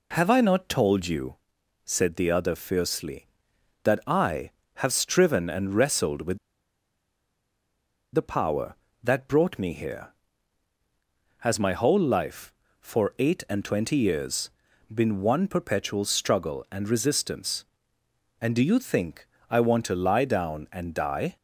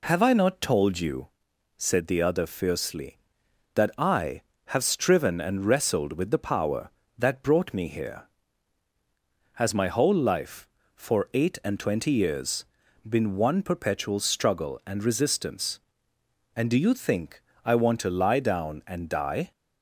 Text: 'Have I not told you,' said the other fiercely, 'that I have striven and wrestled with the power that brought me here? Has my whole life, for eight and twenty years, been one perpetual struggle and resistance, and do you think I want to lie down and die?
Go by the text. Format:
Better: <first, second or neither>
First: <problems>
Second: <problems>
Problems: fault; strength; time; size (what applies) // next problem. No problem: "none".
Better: second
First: pauses between "with" and "the"; strong; at 6.3 s; 1.7 s long // pauses between "think" and "I"; slight; at 19.2 s; 0.20 s long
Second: pauses between "think" and "I"; slight; at 17.4 s; 0.20 s long